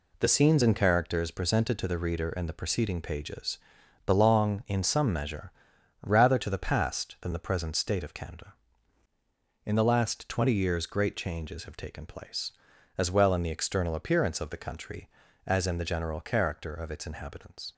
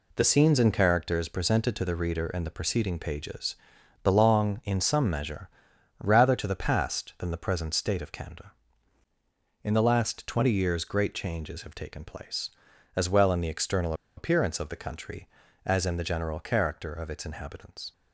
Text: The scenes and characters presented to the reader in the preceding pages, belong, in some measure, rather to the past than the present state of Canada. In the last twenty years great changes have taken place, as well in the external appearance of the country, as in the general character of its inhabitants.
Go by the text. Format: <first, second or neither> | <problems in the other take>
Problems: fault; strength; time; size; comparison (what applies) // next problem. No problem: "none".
first | pauses between "external" and "appearance"; slight; at 13.9 s; 0.23 s long